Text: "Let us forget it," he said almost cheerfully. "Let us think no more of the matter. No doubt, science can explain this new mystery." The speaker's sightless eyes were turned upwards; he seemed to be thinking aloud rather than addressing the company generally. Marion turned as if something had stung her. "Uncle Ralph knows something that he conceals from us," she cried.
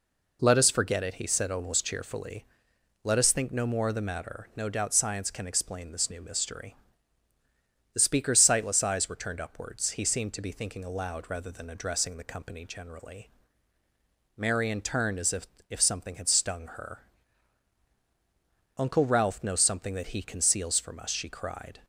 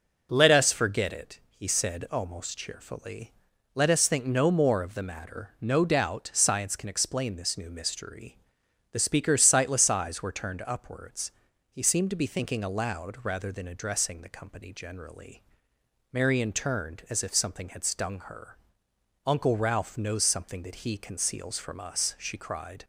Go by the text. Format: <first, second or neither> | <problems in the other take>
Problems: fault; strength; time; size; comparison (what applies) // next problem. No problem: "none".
second | says "if" twice; at 15.6 s